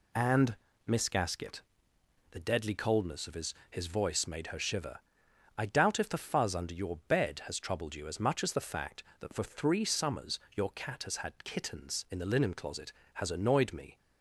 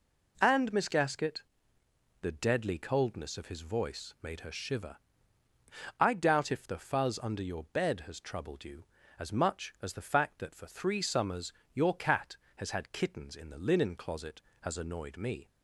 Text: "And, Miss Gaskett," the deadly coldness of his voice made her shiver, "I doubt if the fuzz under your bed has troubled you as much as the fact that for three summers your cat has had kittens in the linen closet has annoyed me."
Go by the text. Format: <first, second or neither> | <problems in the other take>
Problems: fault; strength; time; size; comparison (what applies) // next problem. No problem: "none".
second | says "his" twice; at 3.7 s // pauses between "summers" and "your"; slight; at 10.3 s; 0.16 s long; slight in the second